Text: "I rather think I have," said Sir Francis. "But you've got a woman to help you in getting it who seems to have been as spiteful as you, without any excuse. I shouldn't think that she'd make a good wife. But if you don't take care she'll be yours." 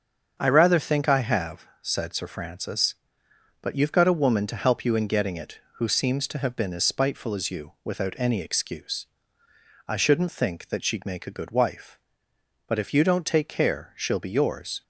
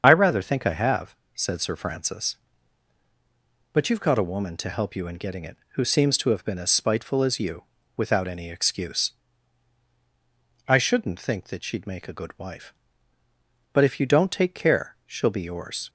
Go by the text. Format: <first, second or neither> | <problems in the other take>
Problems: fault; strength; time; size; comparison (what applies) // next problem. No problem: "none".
first | loses the start of "I"; at 0.0 s; 30 ms // starts louder than the rest; strong; until 1.0 s; 7.5 dB; also in the first